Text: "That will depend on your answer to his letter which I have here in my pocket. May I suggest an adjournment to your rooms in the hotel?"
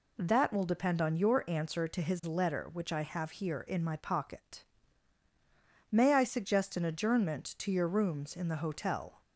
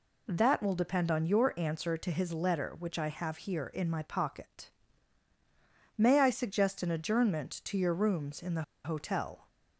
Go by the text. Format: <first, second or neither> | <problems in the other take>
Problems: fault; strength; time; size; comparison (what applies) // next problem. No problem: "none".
first | pauses between "the" and "hotel"; slight; at 8.6 s; 0.20 s long